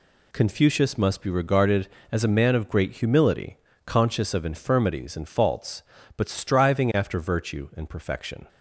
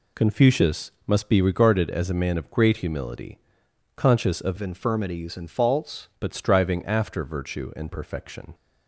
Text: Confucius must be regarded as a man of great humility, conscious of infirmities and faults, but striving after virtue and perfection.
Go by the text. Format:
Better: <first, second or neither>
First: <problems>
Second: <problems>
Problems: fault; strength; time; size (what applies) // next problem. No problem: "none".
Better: first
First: none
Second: pauses between "Confucius" and "must"; slight; at 0.9 s; 0.16 s long // changes voice from "infirmities" to "faults"; from 4.5 to 6.0 s; 1.5 s long